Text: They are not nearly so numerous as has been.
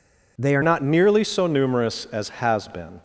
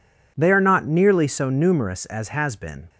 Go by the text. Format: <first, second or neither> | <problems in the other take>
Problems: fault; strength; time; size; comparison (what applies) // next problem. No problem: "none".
second | changes voice at "not"; from 0.6 s on; 2.4 s long